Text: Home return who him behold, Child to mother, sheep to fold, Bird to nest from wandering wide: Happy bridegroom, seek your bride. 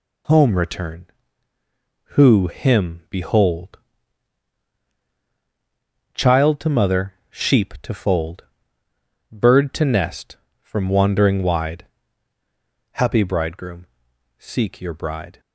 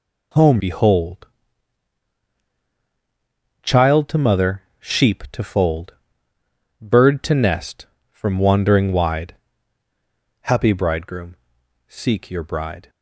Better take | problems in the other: first | skips "return who him"; at 0.5 s

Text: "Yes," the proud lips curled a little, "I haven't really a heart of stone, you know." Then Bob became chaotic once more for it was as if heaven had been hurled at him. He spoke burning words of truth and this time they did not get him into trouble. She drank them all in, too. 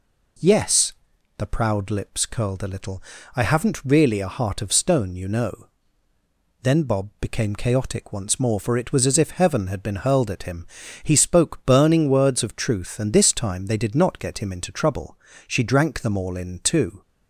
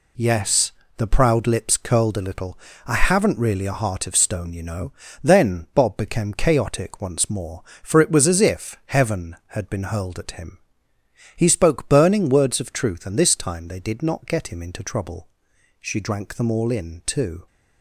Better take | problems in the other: neither | none

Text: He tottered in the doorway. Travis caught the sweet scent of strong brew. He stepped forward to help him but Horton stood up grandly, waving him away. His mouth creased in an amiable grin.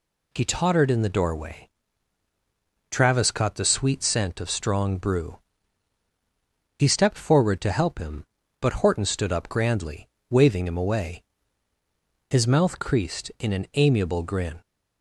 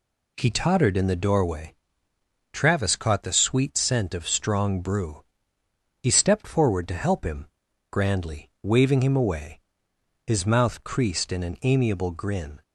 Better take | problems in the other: first | skips "but Horton stood up"; at 7.6 s

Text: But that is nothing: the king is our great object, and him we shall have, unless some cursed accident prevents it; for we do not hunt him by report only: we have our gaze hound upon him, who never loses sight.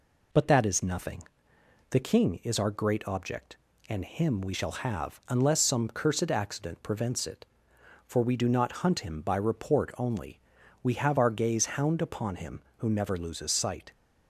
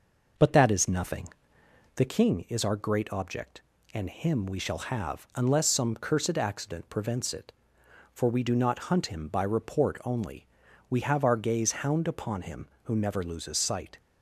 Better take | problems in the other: first | starts louder than the rest; noticeable; until 2.0 s; 5.5 dB

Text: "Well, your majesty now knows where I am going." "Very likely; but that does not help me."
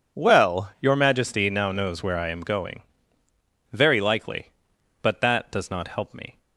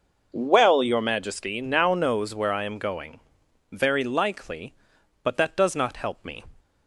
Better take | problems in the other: neither | none

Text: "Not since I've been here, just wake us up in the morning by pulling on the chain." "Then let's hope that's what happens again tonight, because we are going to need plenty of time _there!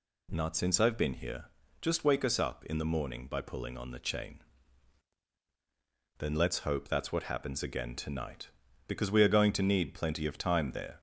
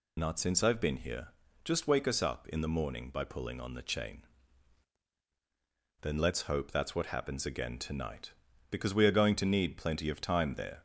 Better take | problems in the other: first | loses the start of "Not"; at 0.1 s; 55 ms

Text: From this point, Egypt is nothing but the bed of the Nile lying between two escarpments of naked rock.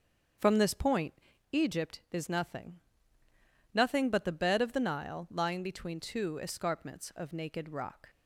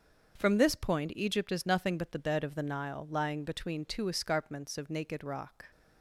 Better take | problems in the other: second | starts louder than the rest; until 1.7 s; 7 dB; also in the second // says "nothing" twice; at 3.7 s

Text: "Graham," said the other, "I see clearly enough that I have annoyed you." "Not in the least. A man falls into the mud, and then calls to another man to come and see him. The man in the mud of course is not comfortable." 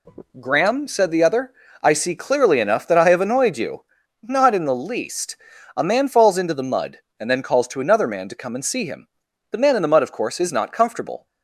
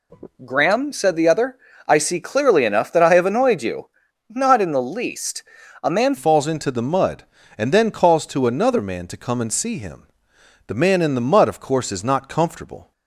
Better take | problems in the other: first | changes voice at "falls"; from 6.1 s on; 6.8 s long

